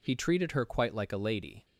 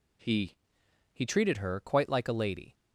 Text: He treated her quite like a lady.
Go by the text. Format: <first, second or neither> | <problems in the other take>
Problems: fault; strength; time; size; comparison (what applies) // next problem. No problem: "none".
first | says "He" twice; at 1.1 s